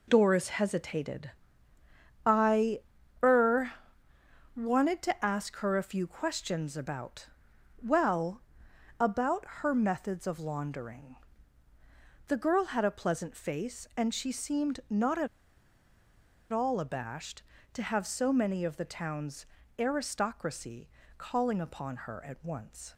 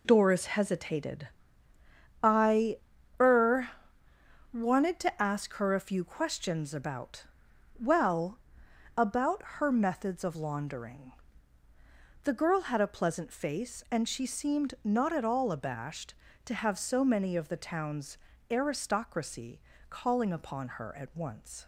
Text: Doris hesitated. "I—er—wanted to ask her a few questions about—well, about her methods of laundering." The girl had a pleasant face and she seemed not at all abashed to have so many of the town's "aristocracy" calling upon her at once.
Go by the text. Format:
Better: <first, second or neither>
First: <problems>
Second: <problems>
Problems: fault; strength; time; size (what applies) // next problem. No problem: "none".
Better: second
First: pauses between "about" and "her"; slight; at 9.4 s; 0.16 s long // pauses between "at" and "all"; at 15.2 s; 1.2 s long // pauses between "town's" and "aristocracy"; slight; at 19.4 s; 0.34 s long // pauses between "aristocracy" and "calling"; slight; at 20.8 s; 0.28 s long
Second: pauses between "about" and "her"; slight; at 9.4 s; 0.16 s long // pauses between "town's" and "aristocracy"; slight; at 18.1 s; 0.34 s long // pauses between "aristocracy" and "calling"; slight; at 19.6 s; 0.28 s long